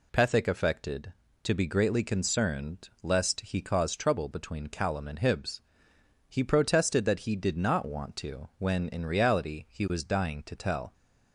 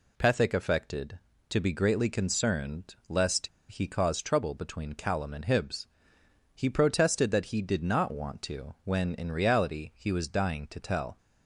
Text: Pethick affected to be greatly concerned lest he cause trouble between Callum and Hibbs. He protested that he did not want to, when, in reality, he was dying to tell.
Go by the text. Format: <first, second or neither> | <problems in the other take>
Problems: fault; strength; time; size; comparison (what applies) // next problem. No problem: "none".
first | pauses between "lest" and "he"; slight; at 3.4 s; 0.21 s long